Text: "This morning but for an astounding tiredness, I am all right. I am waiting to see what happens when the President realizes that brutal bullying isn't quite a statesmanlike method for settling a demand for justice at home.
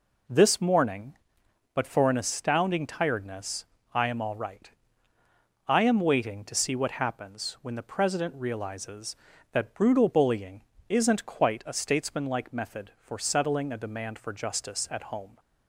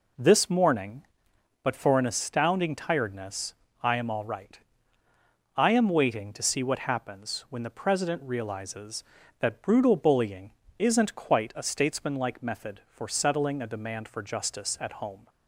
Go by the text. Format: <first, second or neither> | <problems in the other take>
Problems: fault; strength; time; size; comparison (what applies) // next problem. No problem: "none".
neither | pauses between "bullying" and "isn't"; slight; the same in both